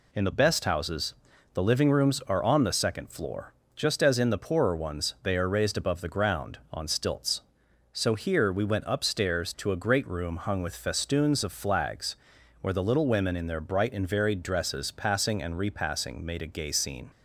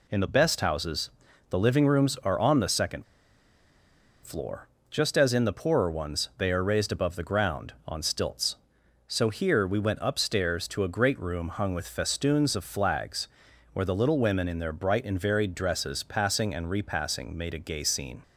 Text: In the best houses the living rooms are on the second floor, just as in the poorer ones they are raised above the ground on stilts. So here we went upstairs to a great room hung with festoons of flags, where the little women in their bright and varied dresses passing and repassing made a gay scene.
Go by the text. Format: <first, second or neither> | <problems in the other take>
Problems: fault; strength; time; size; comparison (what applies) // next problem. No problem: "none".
first | pauses between "houses" and "the"; at 1.0 s; 0.40 s long; also in the first // pauses between "second" and "floor"; at 3.0 s; 1.2 s long